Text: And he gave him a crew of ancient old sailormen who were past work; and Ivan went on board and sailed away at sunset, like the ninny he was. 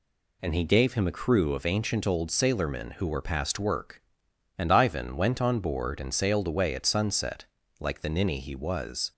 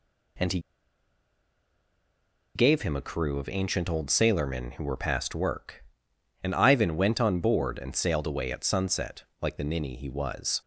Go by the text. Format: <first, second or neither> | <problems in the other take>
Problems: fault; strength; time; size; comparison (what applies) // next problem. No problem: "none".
first | pauses between "he" and "gave"; strong; at 0.5 s; 1.9 s long